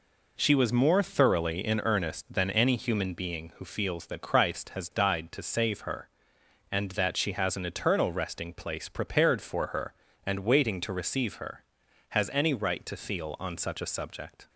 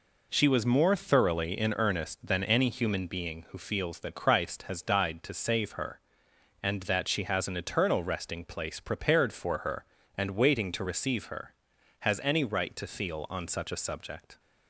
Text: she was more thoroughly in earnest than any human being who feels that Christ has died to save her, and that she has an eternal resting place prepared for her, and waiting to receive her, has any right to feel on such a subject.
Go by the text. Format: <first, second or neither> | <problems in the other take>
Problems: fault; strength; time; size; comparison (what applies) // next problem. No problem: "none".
neither | none